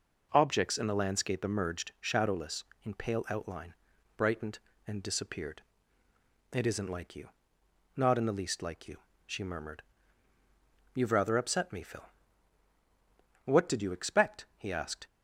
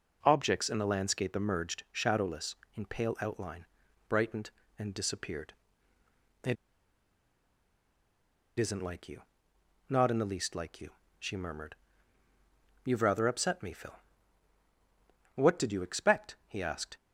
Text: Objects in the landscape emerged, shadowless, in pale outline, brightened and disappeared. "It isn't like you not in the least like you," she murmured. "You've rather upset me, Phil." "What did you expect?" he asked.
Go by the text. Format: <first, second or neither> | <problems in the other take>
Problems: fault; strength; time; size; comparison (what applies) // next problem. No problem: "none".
first | pauses between "It" and "isn't"; strong; at 6.5 s; 2.0 s long // pauses between "you" and "not"; noticeable; at 9.2 s; 0.68 s long; noticeable in the first